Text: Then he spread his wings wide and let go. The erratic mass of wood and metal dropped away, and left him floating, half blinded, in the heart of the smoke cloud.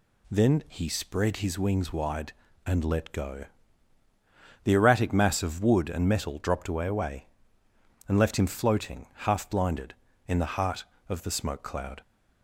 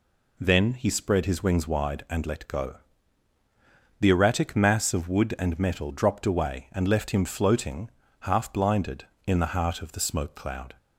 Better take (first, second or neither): second